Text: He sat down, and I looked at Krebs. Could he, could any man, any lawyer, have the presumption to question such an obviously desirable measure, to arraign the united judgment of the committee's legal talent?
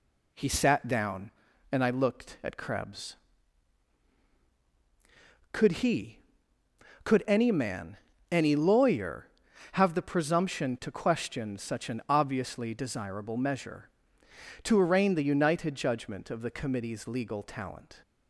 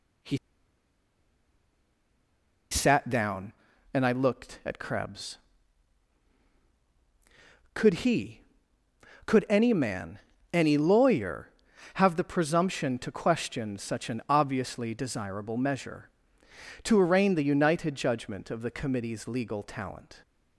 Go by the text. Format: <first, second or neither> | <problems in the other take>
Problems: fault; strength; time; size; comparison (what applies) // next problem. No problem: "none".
first | pauses between "He" and "sat"; strong; at 0.3 s; 2.3 s long